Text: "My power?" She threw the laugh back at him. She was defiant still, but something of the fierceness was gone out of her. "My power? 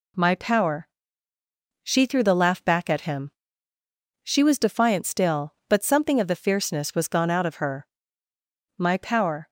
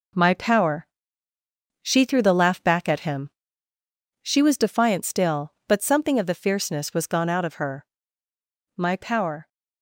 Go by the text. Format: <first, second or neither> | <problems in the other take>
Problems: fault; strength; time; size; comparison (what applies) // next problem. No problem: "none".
first | gets quieter; throughout; 6.5 dB